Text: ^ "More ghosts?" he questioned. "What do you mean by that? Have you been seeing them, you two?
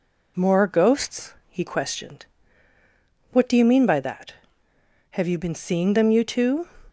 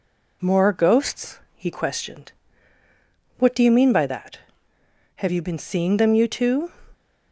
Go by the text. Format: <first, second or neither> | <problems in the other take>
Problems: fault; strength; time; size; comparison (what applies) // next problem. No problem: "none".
neither | none